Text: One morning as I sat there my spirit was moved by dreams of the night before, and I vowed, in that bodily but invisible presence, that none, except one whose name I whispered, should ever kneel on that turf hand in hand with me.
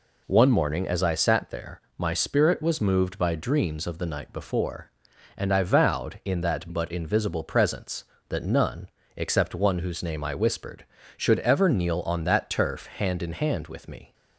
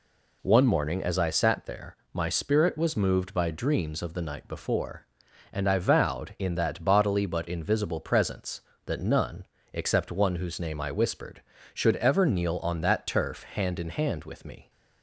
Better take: second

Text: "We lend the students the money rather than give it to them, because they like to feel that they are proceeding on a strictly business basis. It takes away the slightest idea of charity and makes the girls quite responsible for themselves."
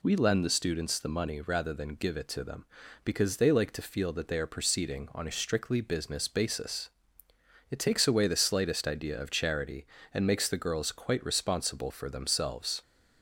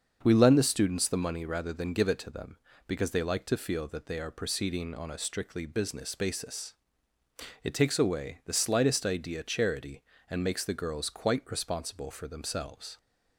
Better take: first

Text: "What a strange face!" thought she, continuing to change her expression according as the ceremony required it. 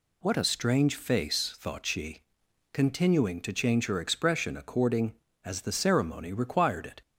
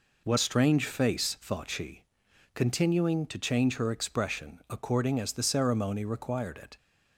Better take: first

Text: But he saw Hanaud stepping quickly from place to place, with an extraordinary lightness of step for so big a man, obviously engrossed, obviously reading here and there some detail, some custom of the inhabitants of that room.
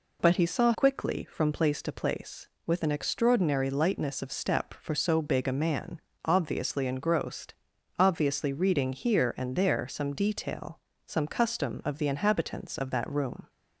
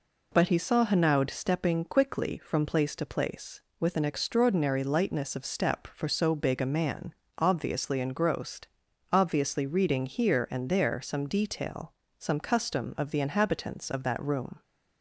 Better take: second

